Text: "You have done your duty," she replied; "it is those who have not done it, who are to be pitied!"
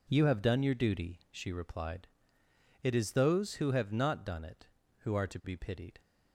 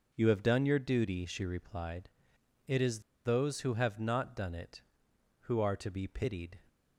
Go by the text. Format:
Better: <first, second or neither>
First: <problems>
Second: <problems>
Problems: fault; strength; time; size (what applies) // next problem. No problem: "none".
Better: first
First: none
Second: pauses between "is" and "those"; slight; at 3.0 s; 0.25 s long